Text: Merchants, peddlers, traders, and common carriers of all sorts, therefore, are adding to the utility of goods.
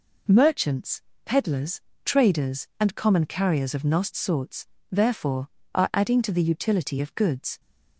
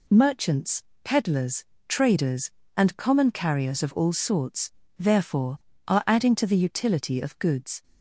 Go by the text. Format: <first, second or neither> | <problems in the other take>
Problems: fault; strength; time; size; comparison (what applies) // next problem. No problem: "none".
second | says "nost" for "all"; at 3.8 s